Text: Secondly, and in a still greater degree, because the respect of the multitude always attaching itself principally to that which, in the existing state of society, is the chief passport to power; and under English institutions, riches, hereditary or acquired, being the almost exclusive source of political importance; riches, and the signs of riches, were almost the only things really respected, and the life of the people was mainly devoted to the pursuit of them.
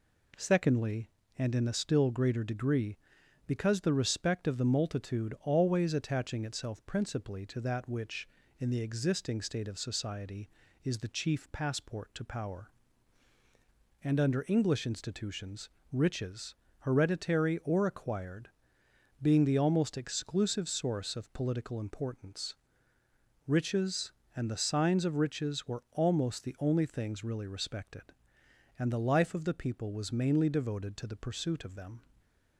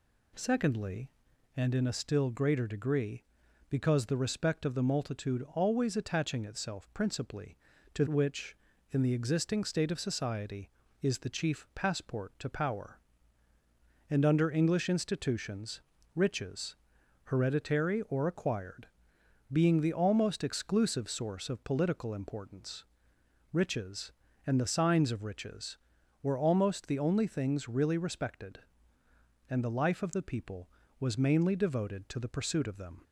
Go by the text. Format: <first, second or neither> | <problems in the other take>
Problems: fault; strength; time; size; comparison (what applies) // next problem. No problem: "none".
first | skips "that"; at 8.0 s